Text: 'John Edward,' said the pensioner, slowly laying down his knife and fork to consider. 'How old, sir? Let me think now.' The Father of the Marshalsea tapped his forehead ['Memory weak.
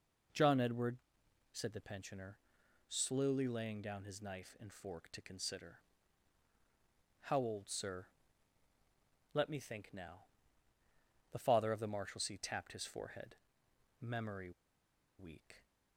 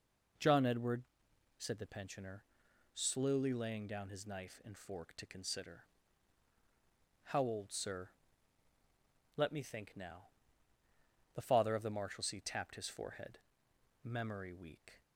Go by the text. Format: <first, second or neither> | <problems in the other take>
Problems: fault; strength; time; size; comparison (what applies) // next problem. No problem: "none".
second | pauses between "forehead" and "Memory"; noticeable; at 13.3 s; 0.64 s long; noticeable in the second // pauses between "Memory" and "weak"; noticeable; at 14.5 s; 0.66 s long